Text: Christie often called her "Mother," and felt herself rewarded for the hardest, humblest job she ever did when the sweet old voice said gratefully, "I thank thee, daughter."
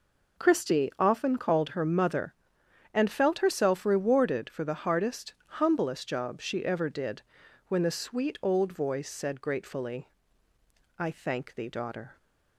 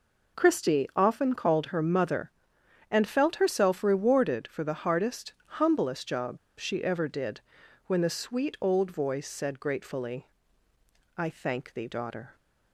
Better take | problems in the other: first | pauses between "job" and "she"; slight; at 6.3 s; 0.21 s long // pauses between "did" and "when"; noticeable; at 7.3 s; 0.48 s long; noticeable in the first

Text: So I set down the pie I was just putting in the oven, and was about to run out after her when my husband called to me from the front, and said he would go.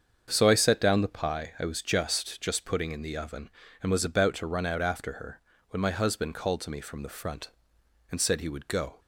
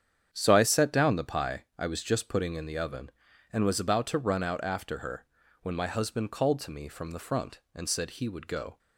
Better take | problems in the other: second | starts louder than the rest; until 1.3 s; 7 dB; strong in the second // says "just" twice; at 2.3 s // pauses between "her" and "when"; slight; at 5.4 s; 0.30 s long; slight in the second

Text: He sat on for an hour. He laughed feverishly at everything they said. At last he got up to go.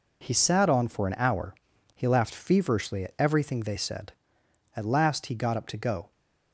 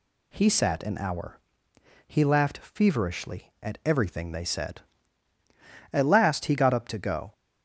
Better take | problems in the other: first | skips "on for"; at 0.8 s

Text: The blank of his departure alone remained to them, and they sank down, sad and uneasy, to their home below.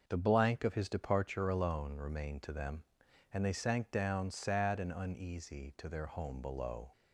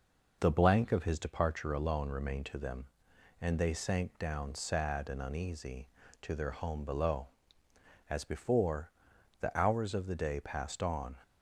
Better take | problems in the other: first | goes on to say "As before the hours of the day passed on"; strong; from 8.0 s on; 3.1 s long

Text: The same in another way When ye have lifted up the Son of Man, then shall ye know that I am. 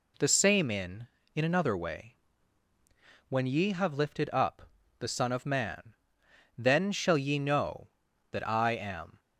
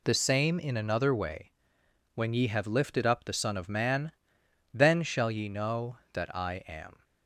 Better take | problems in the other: second | says "in" twice; at 1.3 s // pauses between "way" and "When"; at 2.1 s; 1.1 s long; noticeable in the second // pauses between "up" and "the"; slight; at 4.6 s; 0.30 s long

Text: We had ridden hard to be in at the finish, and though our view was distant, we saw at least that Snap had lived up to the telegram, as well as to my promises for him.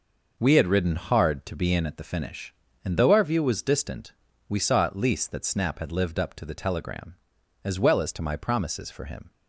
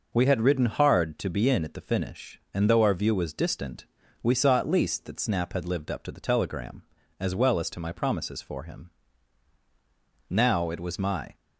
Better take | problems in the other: first | goes on to say "Now it was my"; noticeable; from 10.2 s on; 1.0 s long

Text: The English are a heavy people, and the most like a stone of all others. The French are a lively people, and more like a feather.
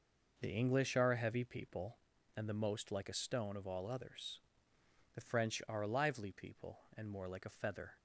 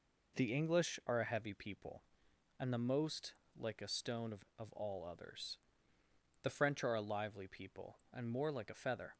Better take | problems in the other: first | pauses between "most" and "like"; slight; at 3.3 s; 0.22 s long // says "of" twice; at 4.5 s

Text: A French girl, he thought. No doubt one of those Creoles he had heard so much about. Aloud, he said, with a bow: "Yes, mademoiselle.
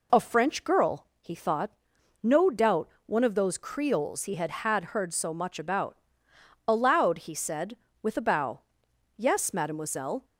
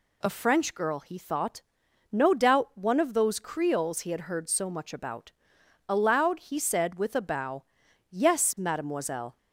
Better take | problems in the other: second | pauses between "doubt" and "one"; slight; at 2.8 s; 0.16 s long // says "had" twice; at 4.5 s

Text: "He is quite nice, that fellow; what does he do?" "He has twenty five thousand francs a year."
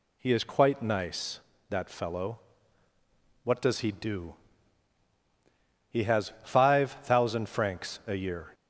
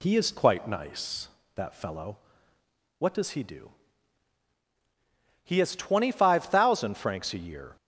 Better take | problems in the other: second | skips "twenty"; at 6.3 s

